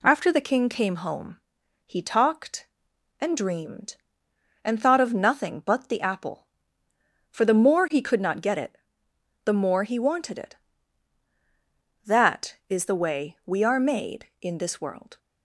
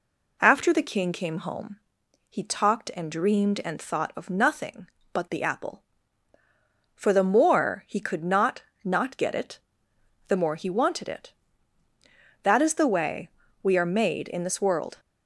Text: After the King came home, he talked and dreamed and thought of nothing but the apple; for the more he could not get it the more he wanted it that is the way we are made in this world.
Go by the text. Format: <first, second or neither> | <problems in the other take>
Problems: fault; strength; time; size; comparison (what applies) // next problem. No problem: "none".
first | says "not" twice; at 8.8 s // pauses between "it" and "the"; noticeable; at 9.5 s; 0.70 s long; noticeable in the first // pauses between "way" and "we"; slight; at 13.2 s; 0.36 s long